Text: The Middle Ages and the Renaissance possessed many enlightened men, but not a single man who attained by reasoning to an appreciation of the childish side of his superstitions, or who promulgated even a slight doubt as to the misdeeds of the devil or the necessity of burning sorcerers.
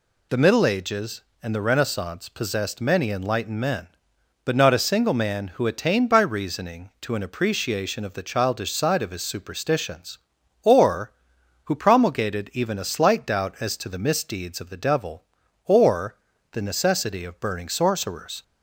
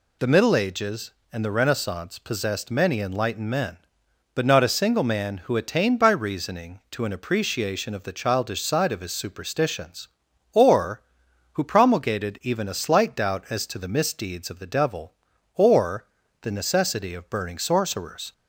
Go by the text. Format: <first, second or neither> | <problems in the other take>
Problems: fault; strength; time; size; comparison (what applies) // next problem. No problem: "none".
neither | pauses between "or" and "the"; slight; the same in both